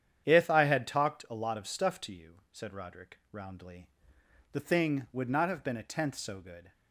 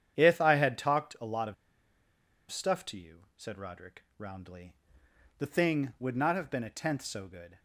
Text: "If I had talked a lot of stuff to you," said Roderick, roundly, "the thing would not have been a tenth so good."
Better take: first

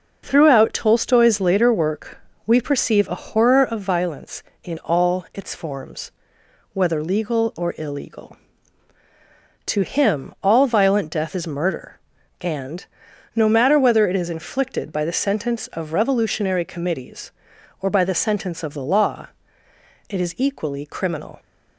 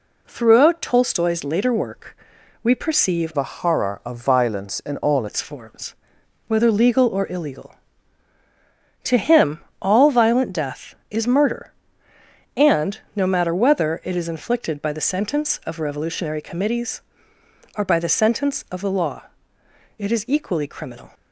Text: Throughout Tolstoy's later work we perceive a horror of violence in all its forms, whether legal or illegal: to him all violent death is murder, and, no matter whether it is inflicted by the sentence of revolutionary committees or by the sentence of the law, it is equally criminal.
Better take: first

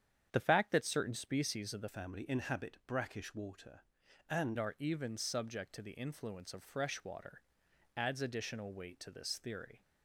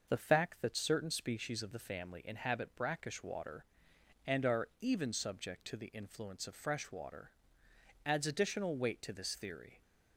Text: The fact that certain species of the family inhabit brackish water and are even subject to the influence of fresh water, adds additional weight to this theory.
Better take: second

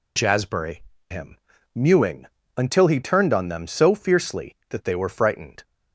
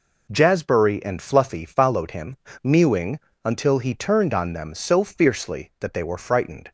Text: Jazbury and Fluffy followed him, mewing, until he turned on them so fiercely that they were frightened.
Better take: second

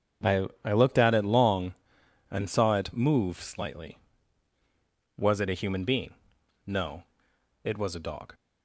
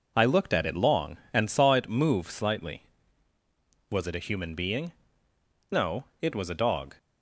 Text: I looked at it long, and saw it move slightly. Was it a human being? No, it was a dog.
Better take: second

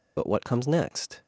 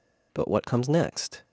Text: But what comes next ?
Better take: second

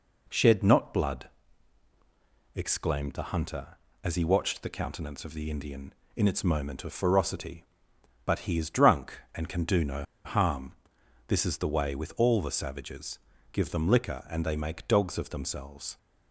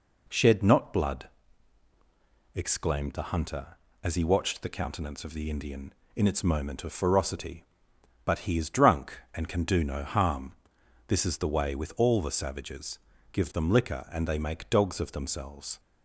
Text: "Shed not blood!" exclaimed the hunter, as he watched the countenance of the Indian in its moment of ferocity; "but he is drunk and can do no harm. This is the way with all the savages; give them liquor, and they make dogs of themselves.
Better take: second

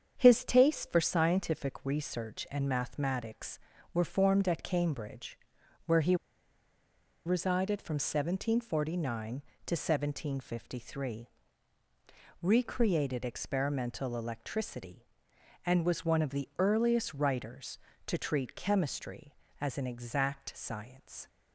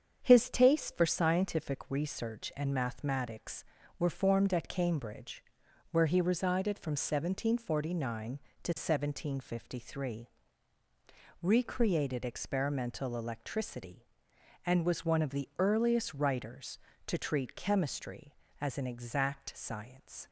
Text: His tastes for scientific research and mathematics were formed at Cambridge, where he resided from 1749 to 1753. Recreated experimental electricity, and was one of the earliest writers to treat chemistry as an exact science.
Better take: second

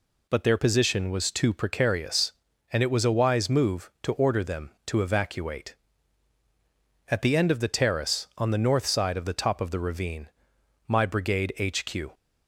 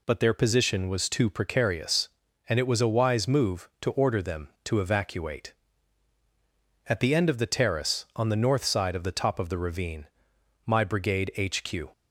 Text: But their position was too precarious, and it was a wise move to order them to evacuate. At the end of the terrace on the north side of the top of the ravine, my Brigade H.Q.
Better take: neither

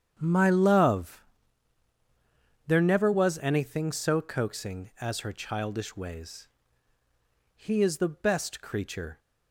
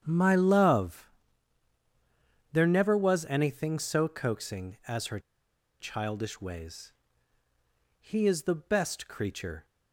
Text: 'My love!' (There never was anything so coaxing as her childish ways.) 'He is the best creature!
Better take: first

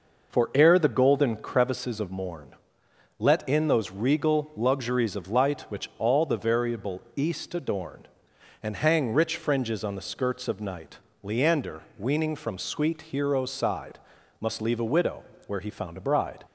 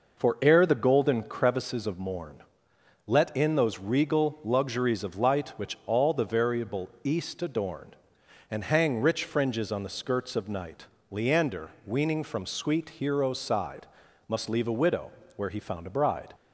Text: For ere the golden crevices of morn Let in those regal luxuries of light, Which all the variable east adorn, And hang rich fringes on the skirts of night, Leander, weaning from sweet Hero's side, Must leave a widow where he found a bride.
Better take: neither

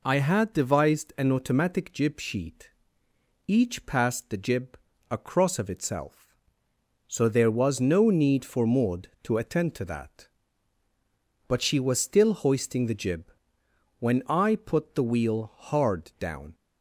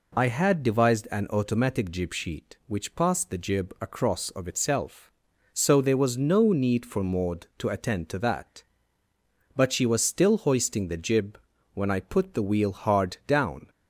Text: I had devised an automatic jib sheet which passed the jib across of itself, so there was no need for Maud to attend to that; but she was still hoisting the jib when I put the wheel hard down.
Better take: second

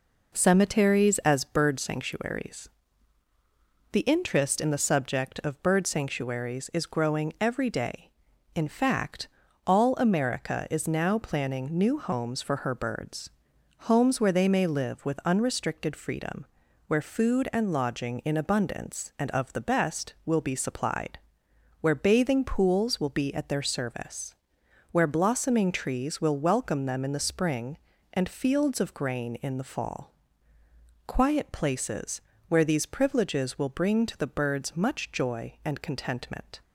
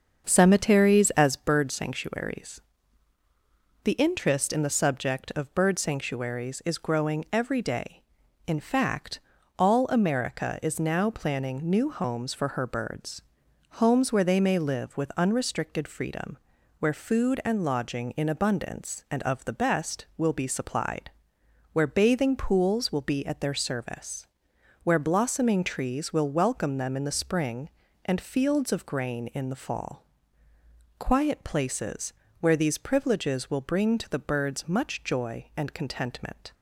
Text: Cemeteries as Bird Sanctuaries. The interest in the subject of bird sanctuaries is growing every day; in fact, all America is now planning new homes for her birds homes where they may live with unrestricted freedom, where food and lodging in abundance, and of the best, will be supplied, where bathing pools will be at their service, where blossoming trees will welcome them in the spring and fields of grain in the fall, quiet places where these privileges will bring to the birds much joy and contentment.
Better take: first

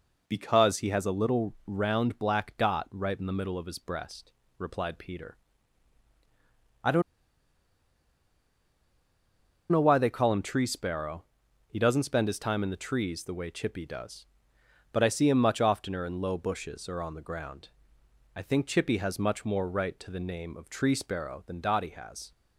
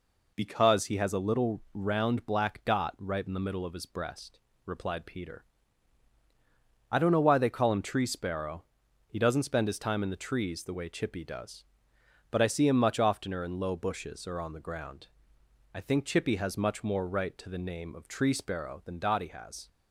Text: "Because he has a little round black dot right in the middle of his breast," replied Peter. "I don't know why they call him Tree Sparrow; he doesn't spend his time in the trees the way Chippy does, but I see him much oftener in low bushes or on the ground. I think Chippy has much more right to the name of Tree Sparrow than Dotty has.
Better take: second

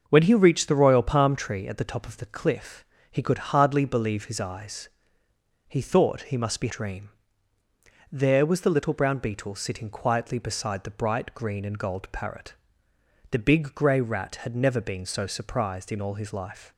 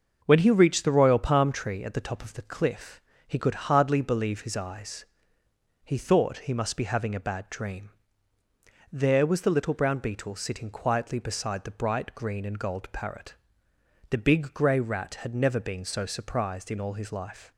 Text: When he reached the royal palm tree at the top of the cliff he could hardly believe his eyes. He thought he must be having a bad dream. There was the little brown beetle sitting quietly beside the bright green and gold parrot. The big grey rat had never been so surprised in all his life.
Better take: second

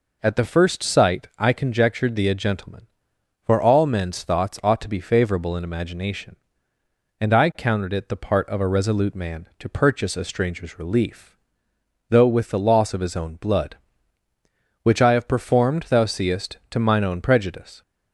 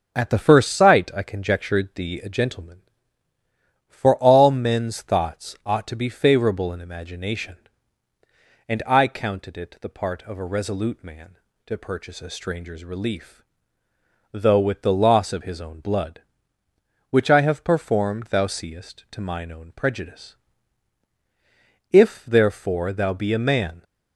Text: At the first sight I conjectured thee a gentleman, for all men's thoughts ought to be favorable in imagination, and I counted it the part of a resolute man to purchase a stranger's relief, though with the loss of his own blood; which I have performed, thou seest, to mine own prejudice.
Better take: first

